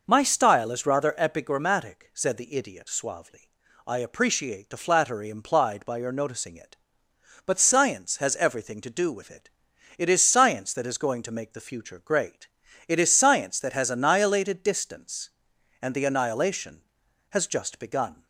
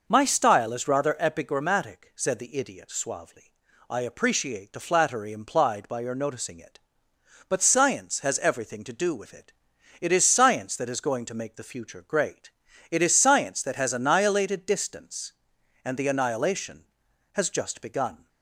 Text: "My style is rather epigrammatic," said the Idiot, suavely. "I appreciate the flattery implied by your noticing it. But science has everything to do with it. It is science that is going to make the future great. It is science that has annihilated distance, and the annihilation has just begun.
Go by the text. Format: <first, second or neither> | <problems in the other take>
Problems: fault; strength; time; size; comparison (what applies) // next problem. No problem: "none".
neither | none